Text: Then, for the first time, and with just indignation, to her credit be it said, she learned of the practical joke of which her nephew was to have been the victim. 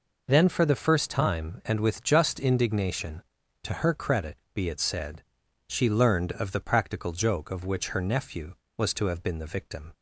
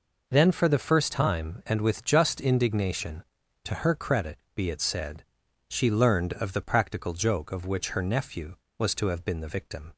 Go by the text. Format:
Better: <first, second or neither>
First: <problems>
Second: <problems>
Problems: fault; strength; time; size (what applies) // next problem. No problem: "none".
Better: neither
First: pauses between "credit" and "be"; slight; at 4.3 s; 0.18 s long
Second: pauses between "credit" and "be"; slight; at 4.3 s; 0.18 s long